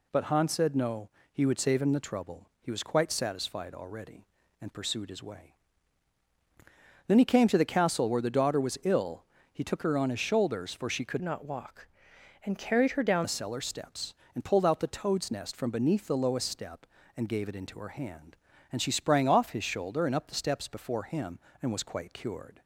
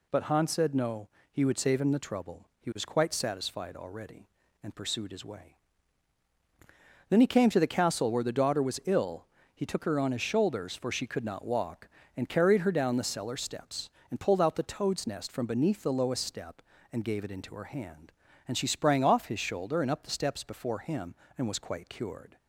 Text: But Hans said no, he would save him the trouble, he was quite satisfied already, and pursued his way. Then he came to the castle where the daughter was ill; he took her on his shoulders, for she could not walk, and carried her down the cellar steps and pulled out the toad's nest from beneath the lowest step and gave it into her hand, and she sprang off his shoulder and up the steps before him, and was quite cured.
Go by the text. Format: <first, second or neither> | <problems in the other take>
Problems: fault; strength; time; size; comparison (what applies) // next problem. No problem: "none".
second | changes voice from "not" to "down"; from 11.2 to 13.2 s; 2.0 s long